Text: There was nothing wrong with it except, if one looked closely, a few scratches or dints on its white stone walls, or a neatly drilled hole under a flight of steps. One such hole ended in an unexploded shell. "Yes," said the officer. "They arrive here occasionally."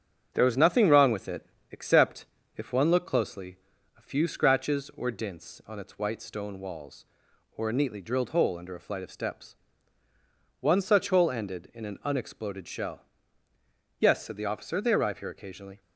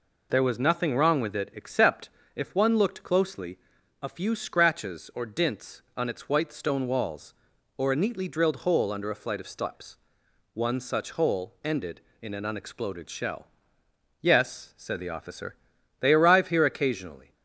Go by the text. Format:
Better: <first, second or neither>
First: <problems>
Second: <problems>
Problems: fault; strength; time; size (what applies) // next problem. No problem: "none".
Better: second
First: gets quieter; noticeable; throughout; 4 dB // pauses between "it" and "except"; slight; at 1.4 s; 0.26 s long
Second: none